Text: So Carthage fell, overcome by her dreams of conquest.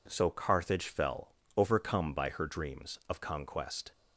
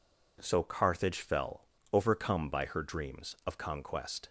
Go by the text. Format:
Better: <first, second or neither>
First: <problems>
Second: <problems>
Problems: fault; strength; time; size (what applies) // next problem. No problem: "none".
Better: neither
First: none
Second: none